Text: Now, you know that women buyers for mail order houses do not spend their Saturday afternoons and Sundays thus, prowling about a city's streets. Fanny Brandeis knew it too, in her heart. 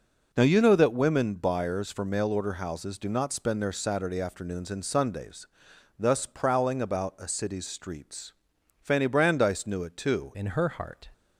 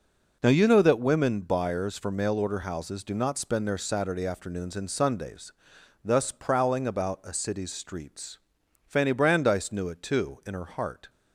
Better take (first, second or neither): second